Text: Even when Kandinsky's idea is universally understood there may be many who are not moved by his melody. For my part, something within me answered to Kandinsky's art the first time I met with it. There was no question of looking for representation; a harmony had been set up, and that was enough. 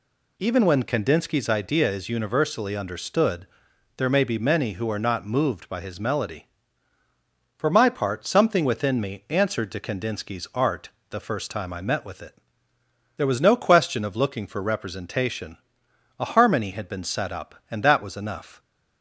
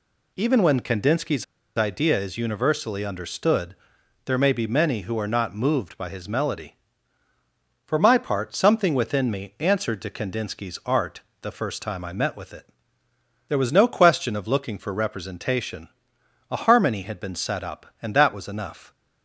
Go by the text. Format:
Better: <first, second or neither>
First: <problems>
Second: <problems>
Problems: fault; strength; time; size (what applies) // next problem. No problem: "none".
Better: first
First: pauses between "understood" and "there"; noticeable; at 3.4 s; 0.52 s long // pauses between "art" and "the"; slight; at 10.8 s; 0.22 s long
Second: pauses between "Kandinsky's" and "idea"; slight; at 1.4 s; 0.32 s long // pauses between "understood" and "there"; noticeable; at 3.7 s; 0.52 s long // pauses between "art" and "the"; slight; at 11.2 s; 0.22 s long